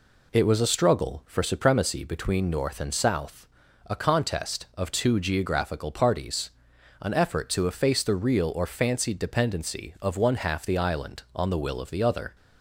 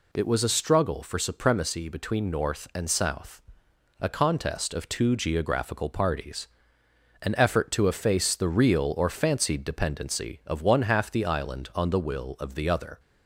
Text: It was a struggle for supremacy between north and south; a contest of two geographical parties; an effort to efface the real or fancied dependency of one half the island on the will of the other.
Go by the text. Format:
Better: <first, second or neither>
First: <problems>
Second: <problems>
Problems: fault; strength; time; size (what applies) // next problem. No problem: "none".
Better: neither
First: none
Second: none